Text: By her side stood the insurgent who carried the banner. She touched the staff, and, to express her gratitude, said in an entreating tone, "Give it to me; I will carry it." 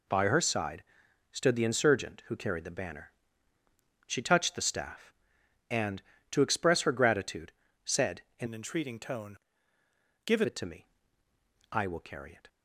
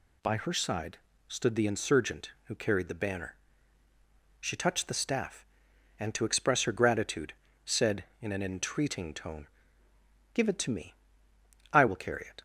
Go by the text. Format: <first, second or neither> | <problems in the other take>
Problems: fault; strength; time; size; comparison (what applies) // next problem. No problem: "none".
second | pauses between "side" and "stood"; noticeable; at 0.8 s; 0.48 s long; slight in the second // changes voice from "an" to "Give"; from 8.4 to 10.4 s; 2.0 s long